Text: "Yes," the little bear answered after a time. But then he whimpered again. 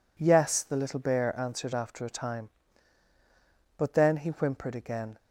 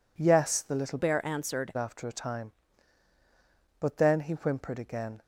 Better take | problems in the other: first | changes voice from "bear" to "answered"; from 0.9 to 1.7 s; 0.8 s long

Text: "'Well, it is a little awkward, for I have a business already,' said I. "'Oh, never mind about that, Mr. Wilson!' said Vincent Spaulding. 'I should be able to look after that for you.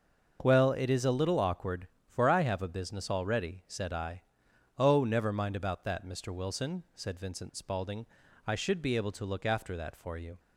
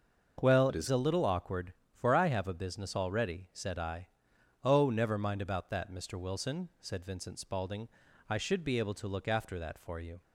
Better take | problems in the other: first | starts louder than the rest; until 1.4 s; 6 dB; noticeable in the first // changes voice from "it" to "is"; from 0.6 to 0.8 s; 0.2 s long

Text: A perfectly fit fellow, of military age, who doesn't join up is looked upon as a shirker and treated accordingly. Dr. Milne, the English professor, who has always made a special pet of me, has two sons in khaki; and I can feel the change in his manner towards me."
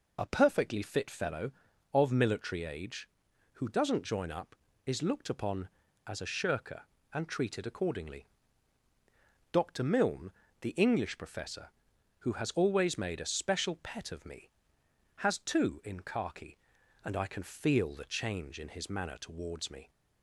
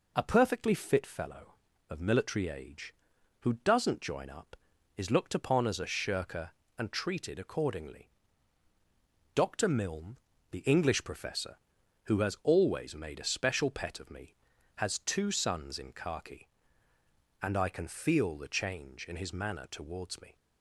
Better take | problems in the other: second | skips "sons"; at 15.8 s

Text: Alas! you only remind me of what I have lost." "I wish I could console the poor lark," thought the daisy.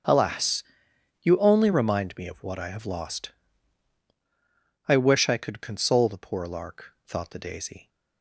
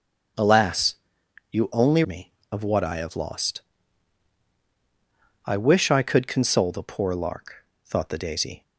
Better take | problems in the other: first | starts louder than the rest; until 1.9 s; 7 dB; strong in the first // skips "remind"; at 2.0 s

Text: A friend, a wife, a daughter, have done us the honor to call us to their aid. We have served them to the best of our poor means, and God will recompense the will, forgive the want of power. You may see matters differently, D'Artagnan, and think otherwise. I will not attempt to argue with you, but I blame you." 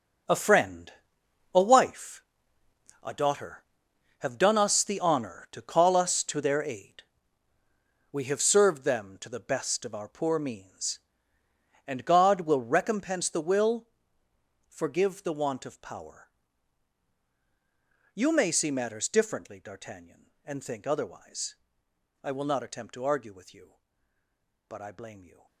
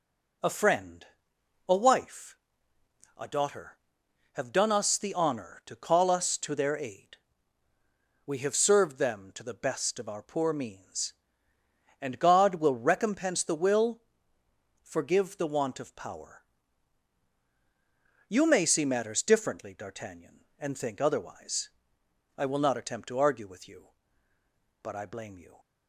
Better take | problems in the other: second | gets quieter; strong; throughout; 12.5 dB

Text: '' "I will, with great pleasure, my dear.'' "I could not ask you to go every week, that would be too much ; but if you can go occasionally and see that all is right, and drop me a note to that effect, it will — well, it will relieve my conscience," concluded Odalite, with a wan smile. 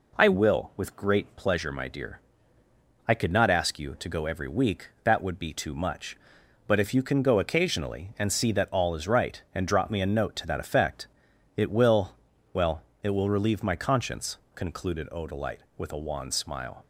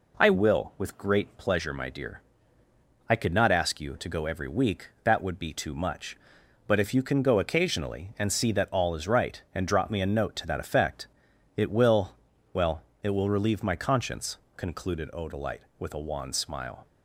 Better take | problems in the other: neither | none

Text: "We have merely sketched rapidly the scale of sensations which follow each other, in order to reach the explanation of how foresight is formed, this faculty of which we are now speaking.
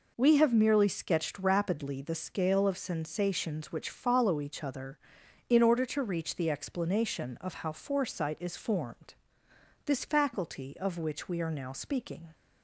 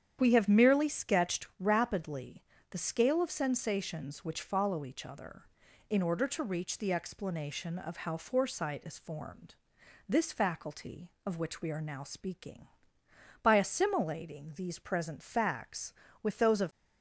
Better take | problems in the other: first | starts louder than the rest; strong; until 1.2 s; 9 dB // pauses between "rapidly" and "the"; slight; at 2.4 s; 0.30 s long // goes on to say "By assimilating these present facts with those of"; strong; from 13.4 s on; 3.2 s long

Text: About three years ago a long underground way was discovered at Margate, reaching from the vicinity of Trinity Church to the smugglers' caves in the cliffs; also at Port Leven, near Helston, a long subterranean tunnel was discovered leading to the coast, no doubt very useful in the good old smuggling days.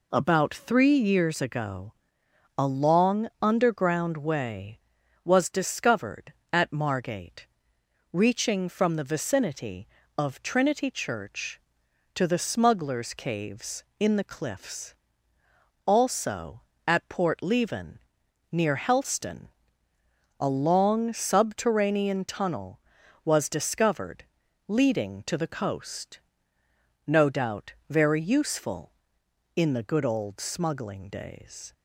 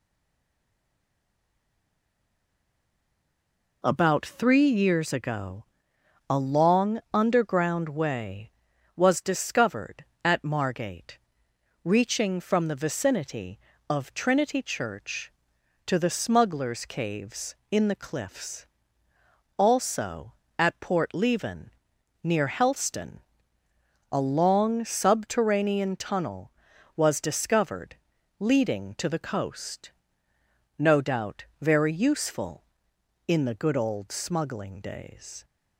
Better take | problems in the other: first | stays silent before the first word; strong; until 3.8 s; 3.8 s long // pauses between "ago" and "a"; noticeable; at 5.6 s; 0.66 s long; noticeable in the first // pauses between "discovered" and "leading"; at 27.9 s; 0.42 s long; also in the first

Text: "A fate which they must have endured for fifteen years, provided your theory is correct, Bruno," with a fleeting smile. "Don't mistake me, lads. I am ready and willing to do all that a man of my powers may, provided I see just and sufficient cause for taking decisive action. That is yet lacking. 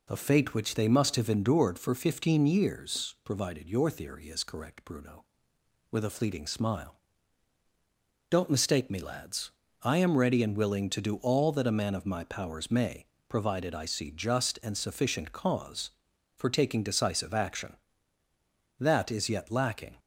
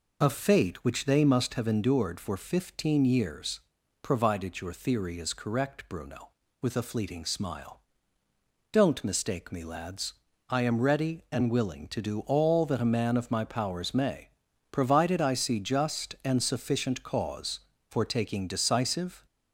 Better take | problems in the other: first | stops before "action That is yet lacking"; at 19.2 s

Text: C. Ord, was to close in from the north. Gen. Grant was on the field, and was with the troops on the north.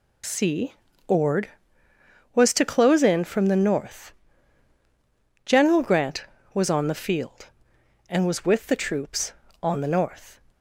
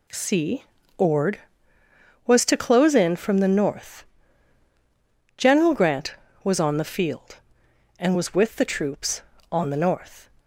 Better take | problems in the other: second | loses the start of "C"; at 0.2 s; 40 ms

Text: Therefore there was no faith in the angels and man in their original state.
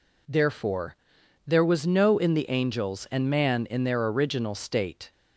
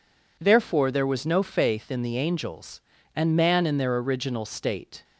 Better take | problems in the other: second | pauses between "Therefore" and "there"; noticeable; at 0.9 s; 0.50 s long // skips "faith"; at 2.1 s

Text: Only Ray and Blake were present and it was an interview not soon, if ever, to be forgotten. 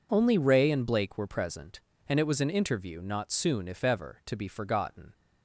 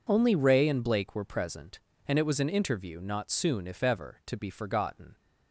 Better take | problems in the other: neither | none

